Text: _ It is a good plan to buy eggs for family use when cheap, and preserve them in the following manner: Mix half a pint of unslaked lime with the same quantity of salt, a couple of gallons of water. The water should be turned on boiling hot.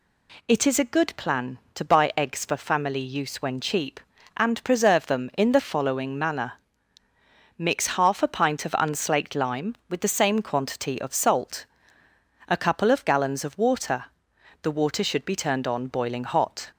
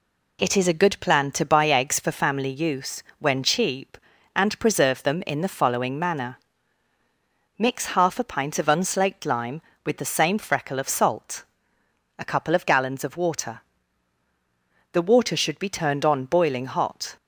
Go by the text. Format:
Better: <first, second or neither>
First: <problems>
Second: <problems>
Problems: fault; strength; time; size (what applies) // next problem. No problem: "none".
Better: first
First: none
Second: pauses between "use" and "when"; slight; at 3.0 s; 0.16 s long // says "freckle" for "quantity"; at 10.3 s